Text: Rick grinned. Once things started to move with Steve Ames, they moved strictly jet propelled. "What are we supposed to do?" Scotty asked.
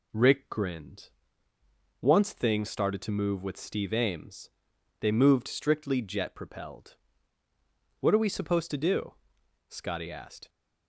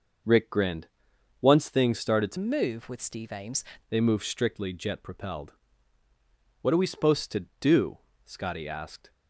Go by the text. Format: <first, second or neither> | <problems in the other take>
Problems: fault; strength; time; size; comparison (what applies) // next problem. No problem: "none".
first | changes voice from "move" to "Ames"; from 2.3 to 3.6 s; 1.3 s long